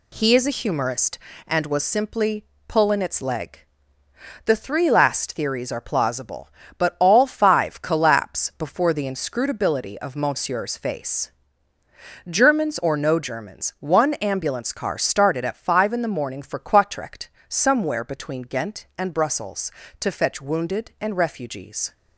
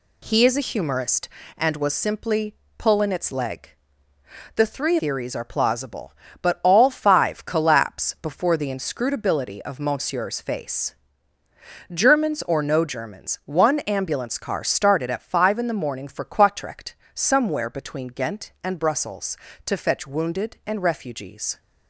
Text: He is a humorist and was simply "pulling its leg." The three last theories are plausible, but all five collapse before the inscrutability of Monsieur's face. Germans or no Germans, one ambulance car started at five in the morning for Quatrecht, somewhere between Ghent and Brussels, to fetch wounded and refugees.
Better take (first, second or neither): first